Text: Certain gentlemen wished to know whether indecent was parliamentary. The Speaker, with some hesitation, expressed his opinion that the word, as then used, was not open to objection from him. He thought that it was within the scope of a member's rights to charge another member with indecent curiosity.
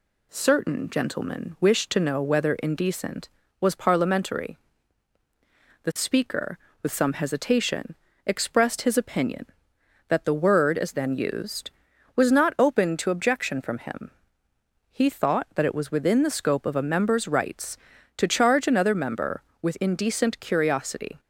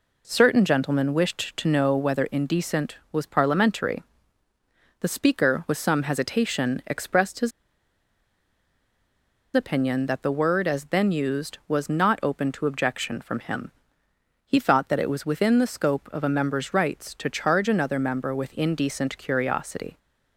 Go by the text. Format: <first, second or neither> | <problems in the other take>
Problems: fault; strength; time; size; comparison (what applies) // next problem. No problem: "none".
first | pauses between "his" and "opinion"; strong; at 7.5 s; 2.0 s long